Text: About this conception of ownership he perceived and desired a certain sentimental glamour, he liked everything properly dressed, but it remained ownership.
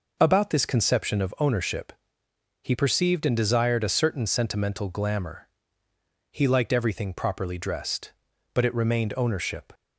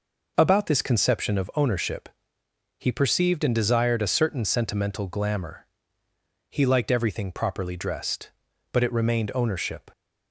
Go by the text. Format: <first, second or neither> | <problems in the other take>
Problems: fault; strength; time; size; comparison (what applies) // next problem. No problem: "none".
neither | pauses between "ownership" and "he"; noticeable; the same in both